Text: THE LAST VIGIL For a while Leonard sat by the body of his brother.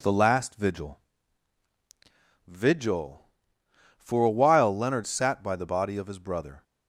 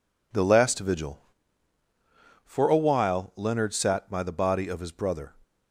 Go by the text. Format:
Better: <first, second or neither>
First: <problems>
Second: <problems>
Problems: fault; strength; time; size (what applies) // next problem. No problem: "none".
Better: second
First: says "VIGIL" twice; at 2.4 s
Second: none